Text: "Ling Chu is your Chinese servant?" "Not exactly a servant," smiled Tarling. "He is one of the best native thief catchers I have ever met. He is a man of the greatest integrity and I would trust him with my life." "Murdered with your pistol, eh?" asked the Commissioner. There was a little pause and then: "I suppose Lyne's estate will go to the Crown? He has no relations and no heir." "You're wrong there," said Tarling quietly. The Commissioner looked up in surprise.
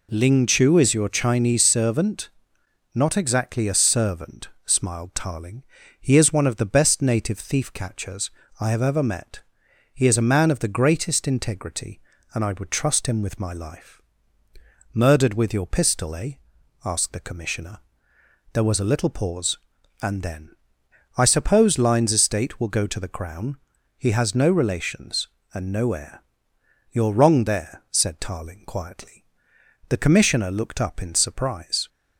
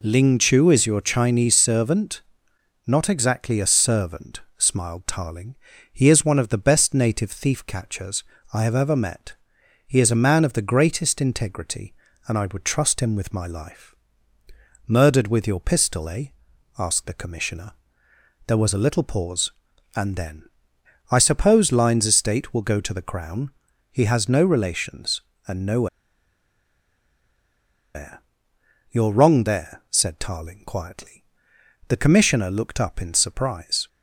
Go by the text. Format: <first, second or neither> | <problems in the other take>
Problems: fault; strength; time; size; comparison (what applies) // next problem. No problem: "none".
first | pauses between "catchers" and "I"; slight; at 8.2 s; 0.28 s long; slight in the first // pauses between "no" and "heir"; strong; at 25.8 s; 2.0 s long